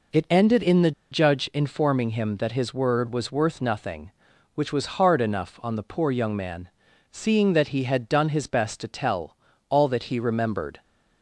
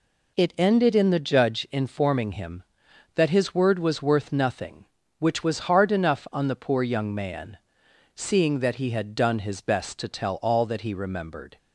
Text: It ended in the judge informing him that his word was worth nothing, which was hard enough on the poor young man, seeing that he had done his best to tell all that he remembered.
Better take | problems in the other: second | pauses between "the" and "judge"; slight; at 0.9 s; 0.20 s long // pauses between "tell" and "all"; slight; at 9.3 s; 0.34 s long

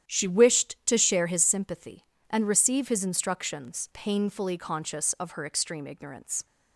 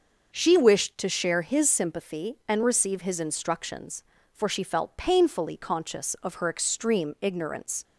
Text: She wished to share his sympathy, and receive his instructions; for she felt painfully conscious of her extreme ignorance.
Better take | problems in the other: second | starts louder than the rest; strong; until 1.1 s; 10 dB // skips "for she felt"; at 3.8 s

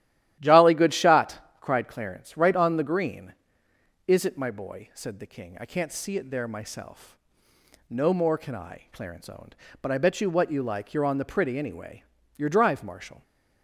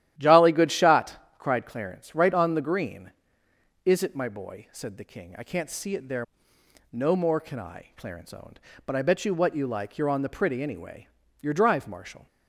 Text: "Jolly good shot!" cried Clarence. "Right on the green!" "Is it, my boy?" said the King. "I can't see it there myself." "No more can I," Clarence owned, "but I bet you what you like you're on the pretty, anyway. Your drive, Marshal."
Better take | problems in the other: first | starts louder than the rest; strong; until 1.1 s; 12.5 dB; strong in the first // skips "myself"; at 6.5 s

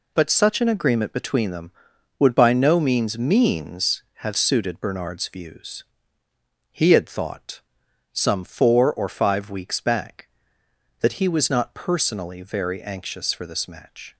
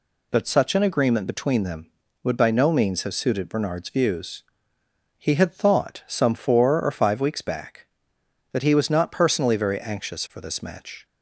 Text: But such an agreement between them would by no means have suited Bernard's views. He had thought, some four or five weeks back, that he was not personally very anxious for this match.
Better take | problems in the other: second | says "means" twice; at 3.1 s

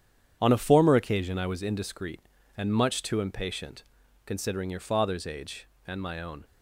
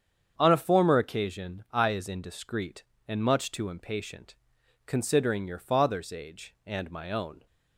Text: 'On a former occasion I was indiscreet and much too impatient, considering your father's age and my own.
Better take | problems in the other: first | starts louder than the rest; strong; until 1.3 s; 7.5 dB; strong in the first // says "is" for "was"; at 1.8 s

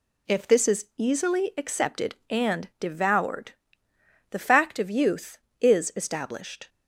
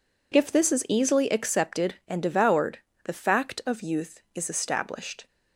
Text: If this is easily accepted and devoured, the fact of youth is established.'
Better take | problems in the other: neither | none

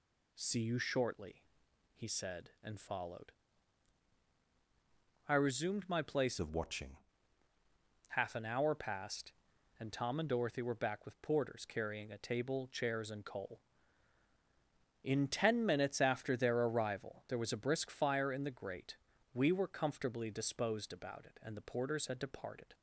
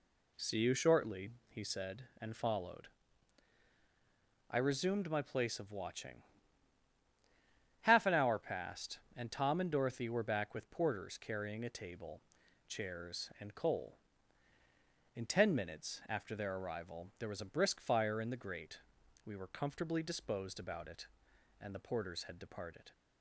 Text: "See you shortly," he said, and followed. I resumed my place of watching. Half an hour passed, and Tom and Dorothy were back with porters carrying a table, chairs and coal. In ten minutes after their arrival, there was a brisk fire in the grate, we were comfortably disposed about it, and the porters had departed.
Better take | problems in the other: second | changes voice from "of" to "watching"; from 6.3 to 6.9 s; 0.6 s long

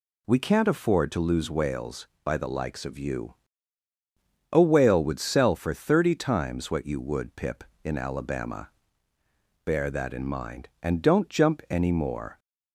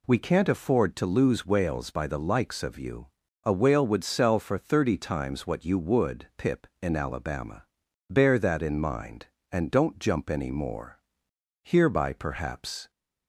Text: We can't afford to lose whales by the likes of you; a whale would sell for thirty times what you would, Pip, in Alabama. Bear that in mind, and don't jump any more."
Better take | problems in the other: first | goes on to say "Hereby perhaps"; noticeable; from 11.6 s on; 1.2 s long

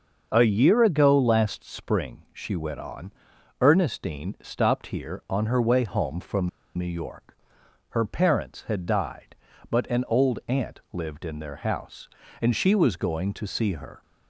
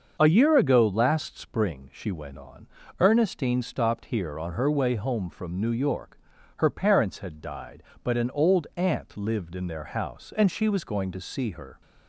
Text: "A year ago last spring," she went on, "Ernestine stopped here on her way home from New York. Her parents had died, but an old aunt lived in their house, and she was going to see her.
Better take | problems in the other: second | starts louder than the rest; until 1.3 s; 6.5 dB; also in the second // pauses between "from" and "New"; slight; at 6.4 s; 0.28 s long

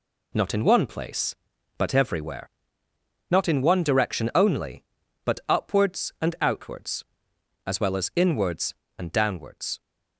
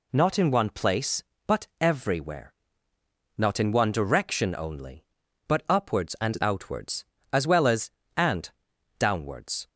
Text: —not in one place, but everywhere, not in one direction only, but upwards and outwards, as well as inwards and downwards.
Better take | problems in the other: first | skips "inwards"; at 8.0 s // pauses between "and" and "downwards"; noticeable; at 8.4 s; 0.48 s long

